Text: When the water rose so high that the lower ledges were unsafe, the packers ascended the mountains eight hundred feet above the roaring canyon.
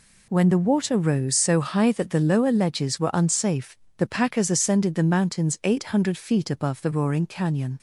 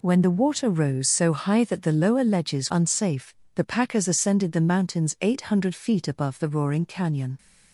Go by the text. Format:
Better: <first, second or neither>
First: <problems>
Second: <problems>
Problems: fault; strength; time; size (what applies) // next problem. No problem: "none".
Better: first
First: none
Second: skips "were"; at 2.7 s